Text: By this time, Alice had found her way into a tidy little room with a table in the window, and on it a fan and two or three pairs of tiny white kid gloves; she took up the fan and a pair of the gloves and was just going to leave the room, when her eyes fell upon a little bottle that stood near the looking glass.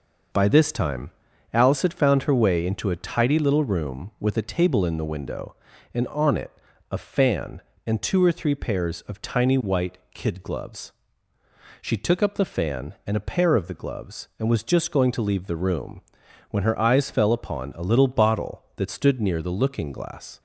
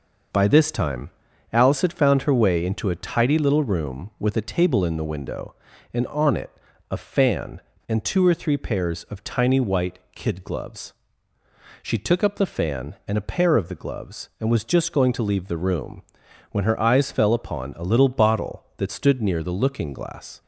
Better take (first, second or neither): neither